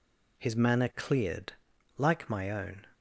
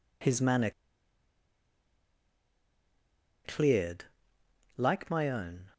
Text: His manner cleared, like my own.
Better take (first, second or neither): first